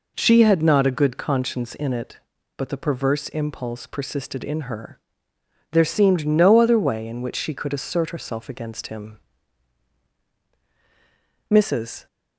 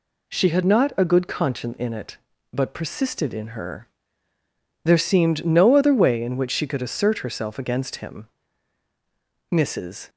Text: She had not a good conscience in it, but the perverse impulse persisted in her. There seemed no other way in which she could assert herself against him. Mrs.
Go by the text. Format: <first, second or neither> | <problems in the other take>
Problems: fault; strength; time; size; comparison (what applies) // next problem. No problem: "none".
first | skips "the perverse impulse"; at 2.7 s